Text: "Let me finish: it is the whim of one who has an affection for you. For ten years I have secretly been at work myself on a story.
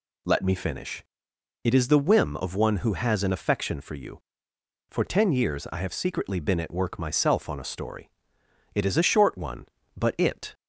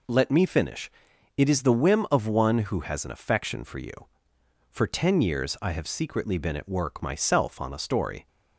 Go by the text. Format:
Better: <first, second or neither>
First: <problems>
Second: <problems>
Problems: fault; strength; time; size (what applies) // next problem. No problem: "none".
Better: second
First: goes on to say "It is a short one but it"; strong; from 8.7 s on; 1.7 s long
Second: none